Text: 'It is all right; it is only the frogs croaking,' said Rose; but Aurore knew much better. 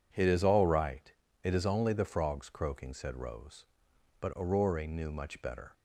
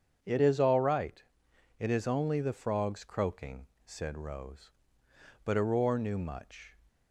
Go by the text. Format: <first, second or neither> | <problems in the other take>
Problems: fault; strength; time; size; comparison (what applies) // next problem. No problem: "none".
first | starts louder than the rest; strong; until 1.2 s; 7.5 dB // stops before "better"; at 6.8 s